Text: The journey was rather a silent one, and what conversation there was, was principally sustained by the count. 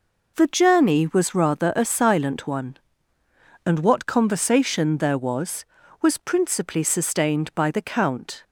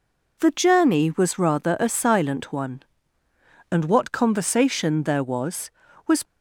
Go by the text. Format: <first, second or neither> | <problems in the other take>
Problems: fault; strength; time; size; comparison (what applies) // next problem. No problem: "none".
first | stops before "principally sustained by the count"; at 6.2 s